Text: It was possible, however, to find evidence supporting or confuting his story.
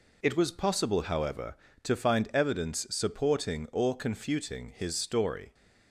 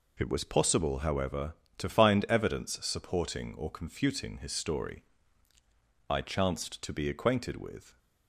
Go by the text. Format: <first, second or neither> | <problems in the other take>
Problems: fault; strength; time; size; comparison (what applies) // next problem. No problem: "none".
first | goes on to say "I chanced to be acquainted with"; strong; from 6.0 s on; 1.8 s long